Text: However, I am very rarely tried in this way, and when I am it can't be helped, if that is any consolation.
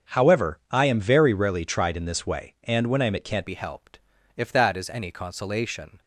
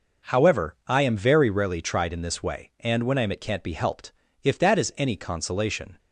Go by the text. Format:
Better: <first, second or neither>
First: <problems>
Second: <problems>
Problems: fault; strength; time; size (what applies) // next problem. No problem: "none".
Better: second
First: starts louder than the rest; strong; until 1.2 s; 7 dB // changes voice at "be"; from 3.4 s on; 2.6 s long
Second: none